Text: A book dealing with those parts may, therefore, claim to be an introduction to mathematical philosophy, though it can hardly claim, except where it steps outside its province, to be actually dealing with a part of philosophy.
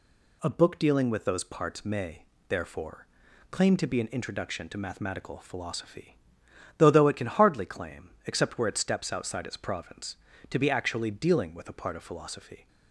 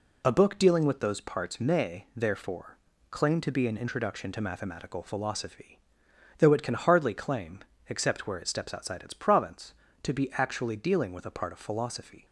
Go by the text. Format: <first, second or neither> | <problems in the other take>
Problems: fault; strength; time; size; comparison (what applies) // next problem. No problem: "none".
second | says "though" twice; at 6.8 s